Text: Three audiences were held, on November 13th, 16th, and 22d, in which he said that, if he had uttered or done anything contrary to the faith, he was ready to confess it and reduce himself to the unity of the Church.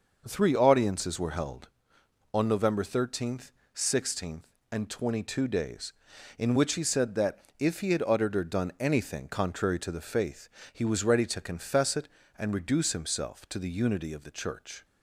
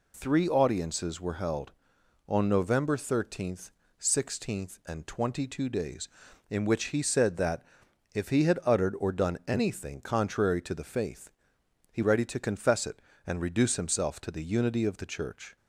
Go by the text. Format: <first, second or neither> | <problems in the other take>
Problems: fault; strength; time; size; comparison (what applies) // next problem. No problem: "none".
first | skips "was"; at 12.0 s